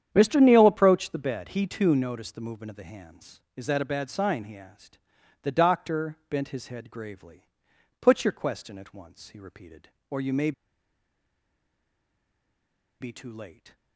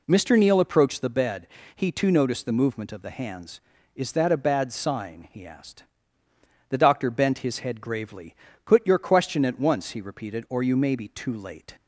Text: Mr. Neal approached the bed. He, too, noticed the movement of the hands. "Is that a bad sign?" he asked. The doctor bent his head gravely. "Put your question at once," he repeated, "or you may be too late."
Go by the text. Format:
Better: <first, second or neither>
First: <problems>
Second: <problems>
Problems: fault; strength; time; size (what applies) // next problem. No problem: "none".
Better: second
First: starts louder than the rest; strong; until 1.1 s; 9 dB // pauses between "may" and "be"; strong; at 10.5 s; 2.4 s long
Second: none